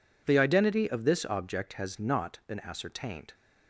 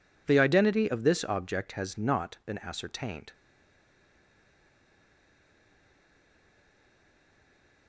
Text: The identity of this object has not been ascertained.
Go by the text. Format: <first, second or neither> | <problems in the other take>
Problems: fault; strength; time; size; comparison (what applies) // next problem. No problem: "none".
first | stays silent after the last word; strong; from 3.3 s on; 4.5 s long